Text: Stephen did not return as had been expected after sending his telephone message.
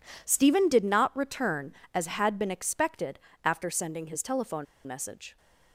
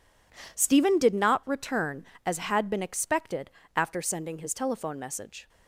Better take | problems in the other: second | pauses between "expected" and "after"; slight; at 3.1 s; 0.24 s long; slight in the second // pauses between "telephone" and "message"; slight; at 4.6 s; 0.19 s long

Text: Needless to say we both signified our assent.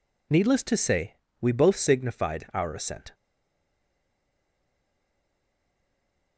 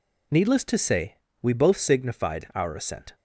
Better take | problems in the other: second | pauses between "say" and "we"; slight; at 1.1 s; 0.28 s long; slight in the second // stays silent after the last word; strong; from 3.1 s on; 3.2 s long

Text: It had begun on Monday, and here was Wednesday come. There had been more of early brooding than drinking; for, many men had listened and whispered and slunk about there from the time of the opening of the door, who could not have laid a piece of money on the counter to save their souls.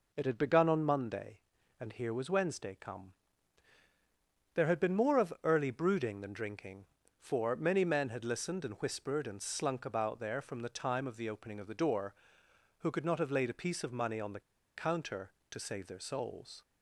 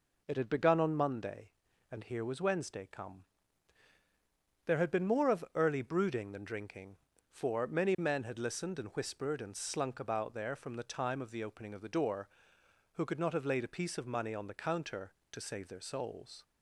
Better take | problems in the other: second | pauses between "the" and "counter"; slight; at 14.4 s; 0.35 s long

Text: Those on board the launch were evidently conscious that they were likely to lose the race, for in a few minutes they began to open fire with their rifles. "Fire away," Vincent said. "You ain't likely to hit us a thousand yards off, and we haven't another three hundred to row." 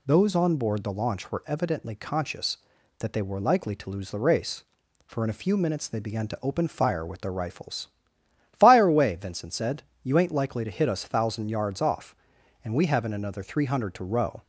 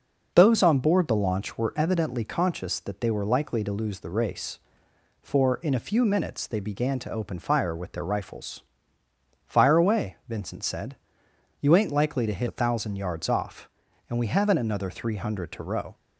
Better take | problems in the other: first | skips "us"; at 12.4 s

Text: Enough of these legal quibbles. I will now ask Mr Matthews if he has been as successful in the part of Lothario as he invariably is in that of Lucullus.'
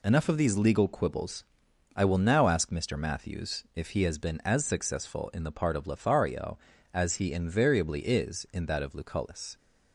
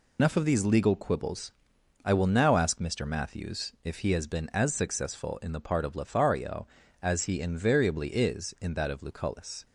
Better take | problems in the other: first | loses the start of "Enough"; at 0.1 s; 80 ms

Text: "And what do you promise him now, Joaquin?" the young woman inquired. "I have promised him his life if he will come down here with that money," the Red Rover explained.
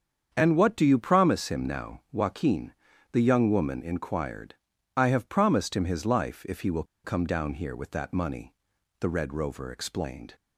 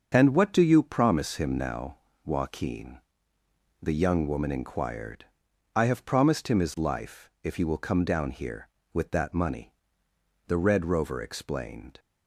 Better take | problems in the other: second | starts louder than the rest; strong; until 1.3 s; 7.5 dB; also in the second // pauses between "will" and "come"; slight; at 6.8 s; 0.20 s long

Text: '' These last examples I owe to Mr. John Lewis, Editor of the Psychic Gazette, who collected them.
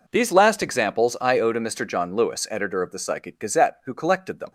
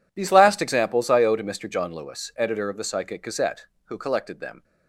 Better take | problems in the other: neither | none

